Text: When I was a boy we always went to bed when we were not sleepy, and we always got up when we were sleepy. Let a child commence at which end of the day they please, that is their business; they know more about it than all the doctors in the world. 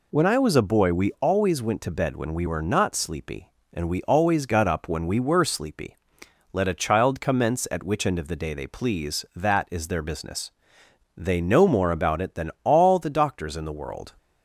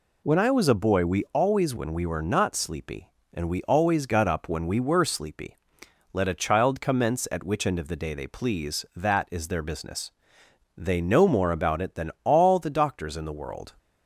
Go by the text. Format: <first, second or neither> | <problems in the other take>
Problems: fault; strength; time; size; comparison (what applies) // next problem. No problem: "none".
first | skips "went to bed"; at 1.7 s